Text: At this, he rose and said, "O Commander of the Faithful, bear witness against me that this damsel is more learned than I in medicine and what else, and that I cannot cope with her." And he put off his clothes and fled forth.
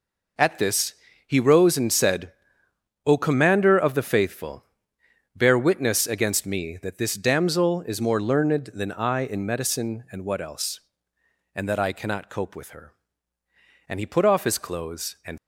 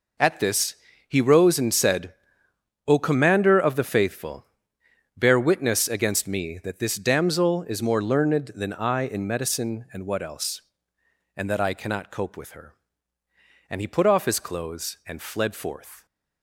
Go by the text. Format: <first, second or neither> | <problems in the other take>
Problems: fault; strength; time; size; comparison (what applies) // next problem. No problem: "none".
second | stops before "fled forth"; at 15.3 s